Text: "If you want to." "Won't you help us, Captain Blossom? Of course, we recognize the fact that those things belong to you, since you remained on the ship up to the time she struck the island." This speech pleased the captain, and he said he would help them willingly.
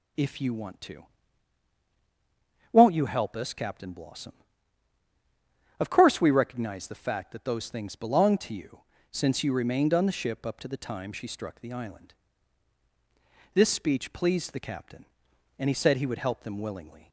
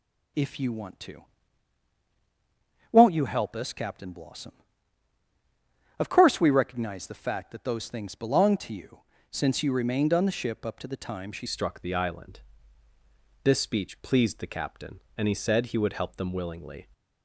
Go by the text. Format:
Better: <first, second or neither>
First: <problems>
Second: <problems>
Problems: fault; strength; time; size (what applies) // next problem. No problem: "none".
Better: first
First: starts louder than the rest; until 2.8 s; 7 dB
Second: starts louder than the rest; until 3.0 s; 6.5 dB // changes voice at "struck"; from 11.4 s on; 5.4 s long